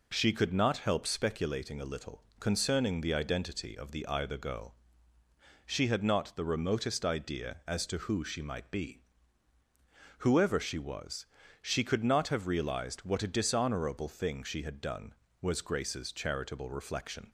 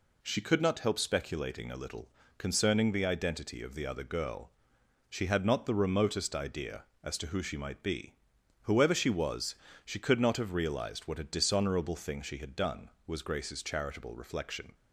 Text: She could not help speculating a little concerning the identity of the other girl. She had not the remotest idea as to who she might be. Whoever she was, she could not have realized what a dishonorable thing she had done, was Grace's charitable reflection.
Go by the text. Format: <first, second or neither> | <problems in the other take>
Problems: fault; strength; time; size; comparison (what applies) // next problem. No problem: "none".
second | pauses between "little" and "concerning"; slight; at 2.2 s; 0.16 s long; slight in the second // says "either" for "other"; at 4.0 s